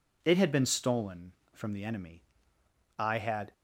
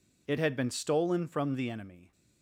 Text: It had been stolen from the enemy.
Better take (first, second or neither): second